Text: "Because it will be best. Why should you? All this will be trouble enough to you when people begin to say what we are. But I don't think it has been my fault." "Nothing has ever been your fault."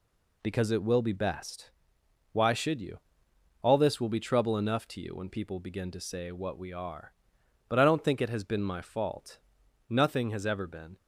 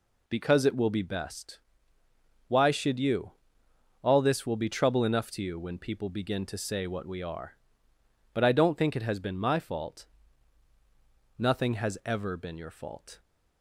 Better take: second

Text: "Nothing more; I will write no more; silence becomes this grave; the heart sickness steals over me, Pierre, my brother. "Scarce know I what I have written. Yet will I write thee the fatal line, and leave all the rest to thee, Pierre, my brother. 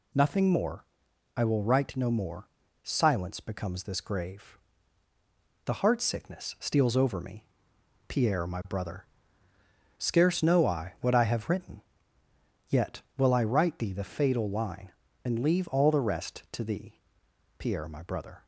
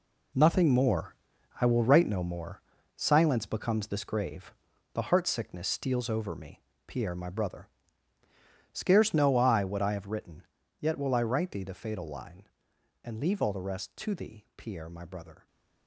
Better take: first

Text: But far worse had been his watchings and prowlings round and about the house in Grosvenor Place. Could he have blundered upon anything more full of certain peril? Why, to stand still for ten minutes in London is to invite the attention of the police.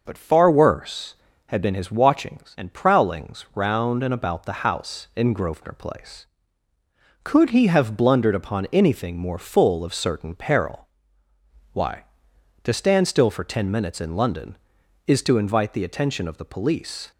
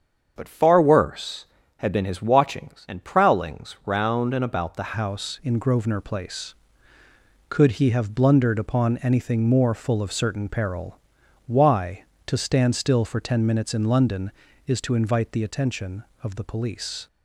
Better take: first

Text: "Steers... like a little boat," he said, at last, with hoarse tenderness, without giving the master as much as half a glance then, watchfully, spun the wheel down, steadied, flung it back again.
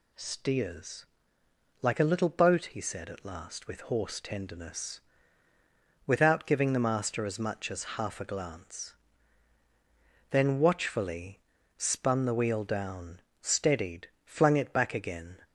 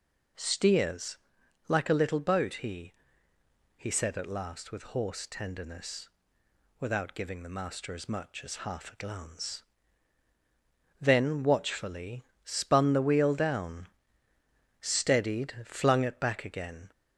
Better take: first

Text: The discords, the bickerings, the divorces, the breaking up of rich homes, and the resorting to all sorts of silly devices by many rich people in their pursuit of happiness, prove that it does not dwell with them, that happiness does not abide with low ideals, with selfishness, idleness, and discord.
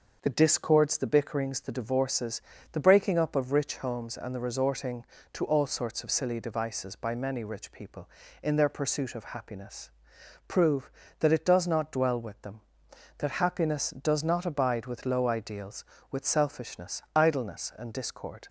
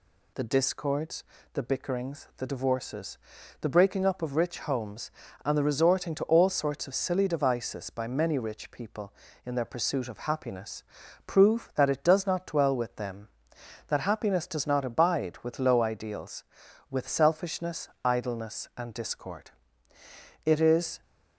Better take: first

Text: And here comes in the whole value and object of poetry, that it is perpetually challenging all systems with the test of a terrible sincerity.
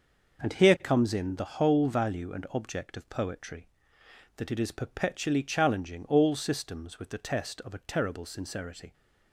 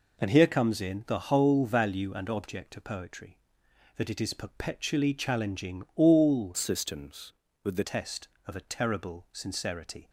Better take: first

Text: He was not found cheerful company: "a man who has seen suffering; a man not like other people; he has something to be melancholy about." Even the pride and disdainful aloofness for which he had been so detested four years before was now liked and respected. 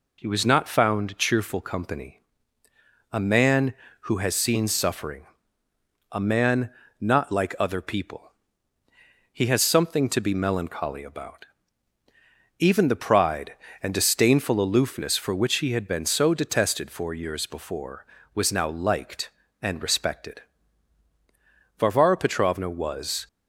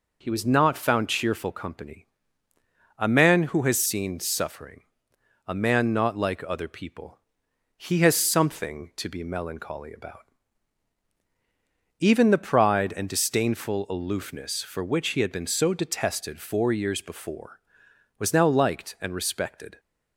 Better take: second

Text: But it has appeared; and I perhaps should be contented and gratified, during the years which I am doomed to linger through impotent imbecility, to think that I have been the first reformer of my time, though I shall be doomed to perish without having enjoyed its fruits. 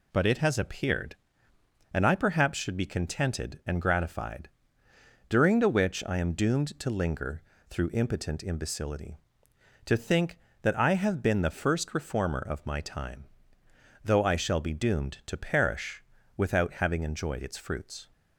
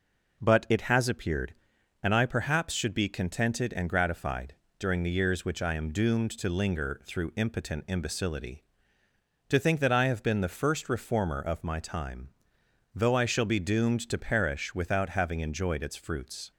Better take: second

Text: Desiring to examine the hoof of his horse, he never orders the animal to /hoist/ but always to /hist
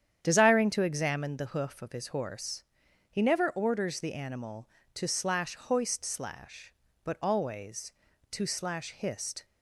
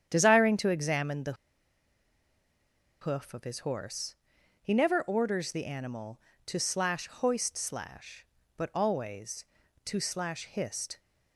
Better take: first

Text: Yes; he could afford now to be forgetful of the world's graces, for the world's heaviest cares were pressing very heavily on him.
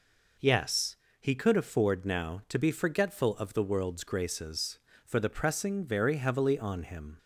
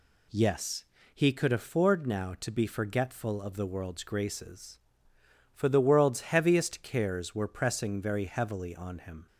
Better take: second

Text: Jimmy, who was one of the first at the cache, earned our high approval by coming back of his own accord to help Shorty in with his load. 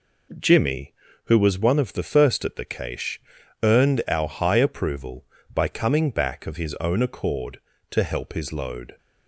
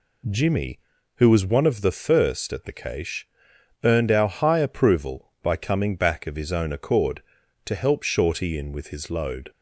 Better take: second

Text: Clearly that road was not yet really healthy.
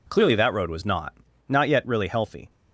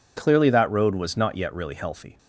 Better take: second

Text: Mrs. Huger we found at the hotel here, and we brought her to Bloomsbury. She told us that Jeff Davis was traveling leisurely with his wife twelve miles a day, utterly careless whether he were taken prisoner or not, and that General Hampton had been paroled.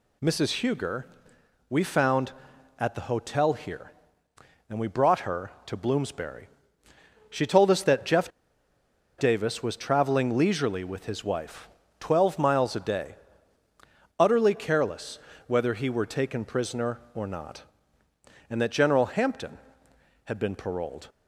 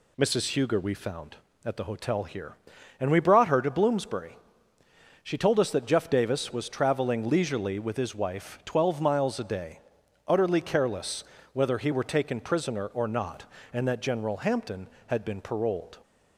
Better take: second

